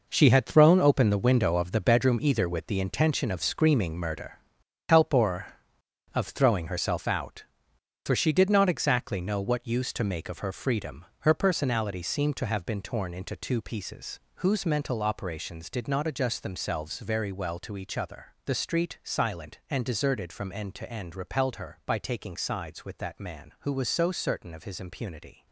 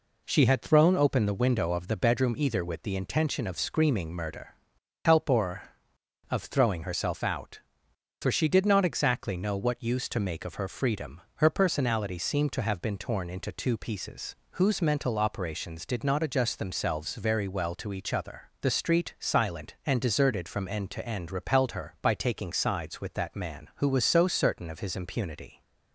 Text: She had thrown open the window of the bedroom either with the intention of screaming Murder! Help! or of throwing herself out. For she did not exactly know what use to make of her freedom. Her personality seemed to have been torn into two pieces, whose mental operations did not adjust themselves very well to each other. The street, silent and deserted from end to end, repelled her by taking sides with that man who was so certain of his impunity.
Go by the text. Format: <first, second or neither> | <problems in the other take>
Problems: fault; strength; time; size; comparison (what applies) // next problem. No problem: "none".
second | gets quieter; strong; throughout; 10.5 dB